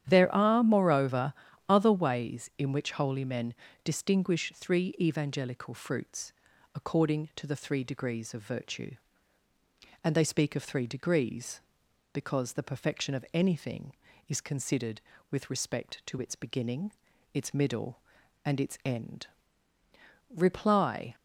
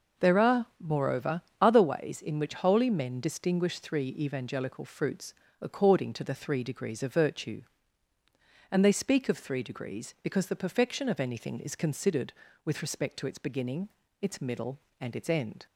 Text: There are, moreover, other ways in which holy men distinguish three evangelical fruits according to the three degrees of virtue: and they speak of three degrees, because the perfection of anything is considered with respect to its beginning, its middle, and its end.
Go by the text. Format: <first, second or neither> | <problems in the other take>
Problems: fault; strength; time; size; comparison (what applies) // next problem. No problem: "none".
second | starts louder than the rest; strong; until 1.0 s; 9.5 dB // pauses between "men" and "distinguish"; slight; at 3.5 s; 0.30 s long // pauses between "fruits" and "according"; at 6.3 s; 0.42 s long; slight in the second // goes on to say "Reply"; noticeable; from 20.3 s on; 0.80 s long